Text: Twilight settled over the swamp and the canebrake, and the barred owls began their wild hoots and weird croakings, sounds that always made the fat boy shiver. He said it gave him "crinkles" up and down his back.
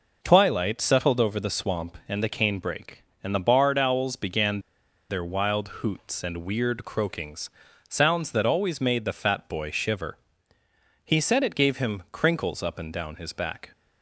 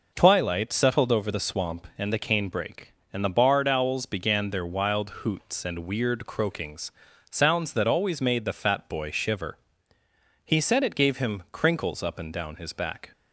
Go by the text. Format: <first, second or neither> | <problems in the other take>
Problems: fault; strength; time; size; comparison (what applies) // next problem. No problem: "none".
second | pauses between "began" and "their"; noticeable; at 4.6 s; 0.48 s long